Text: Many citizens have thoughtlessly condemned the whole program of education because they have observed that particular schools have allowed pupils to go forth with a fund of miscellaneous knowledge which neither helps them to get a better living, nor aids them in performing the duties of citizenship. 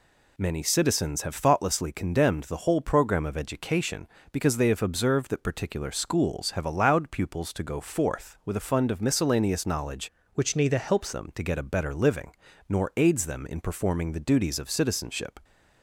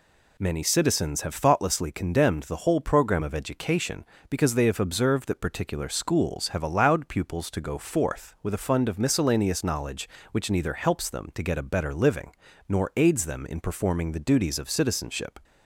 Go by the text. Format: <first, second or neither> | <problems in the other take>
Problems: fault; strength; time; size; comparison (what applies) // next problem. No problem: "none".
second | changes voice from "which" to "helps"; from 10.3 to 11.1 s; 0.8 s long